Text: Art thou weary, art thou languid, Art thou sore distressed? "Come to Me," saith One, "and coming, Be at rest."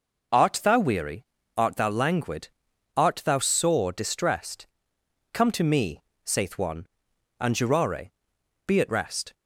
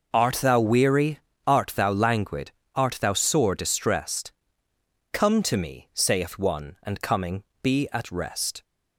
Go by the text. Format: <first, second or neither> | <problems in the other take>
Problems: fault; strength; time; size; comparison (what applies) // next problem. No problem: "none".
second | says "jurare" for "coming"; at 7.5 s